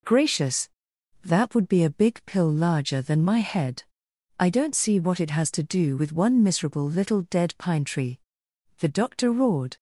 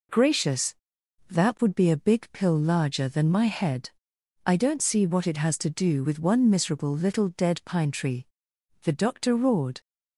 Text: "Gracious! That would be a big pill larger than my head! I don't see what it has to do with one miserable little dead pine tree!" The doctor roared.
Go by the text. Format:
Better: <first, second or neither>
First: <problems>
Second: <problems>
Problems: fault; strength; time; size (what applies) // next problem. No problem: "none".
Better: neither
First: none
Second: none